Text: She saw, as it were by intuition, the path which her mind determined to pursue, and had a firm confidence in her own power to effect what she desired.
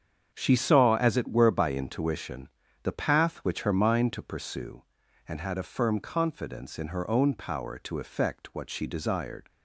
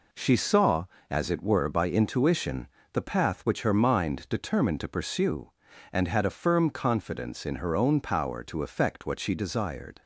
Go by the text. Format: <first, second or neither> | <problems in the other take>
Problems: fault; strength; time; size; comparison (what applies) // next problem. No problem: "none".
second | starts louder than the rest; strong; until 1.3 s; 7.5 dB // skips "determined"; at 4.1 s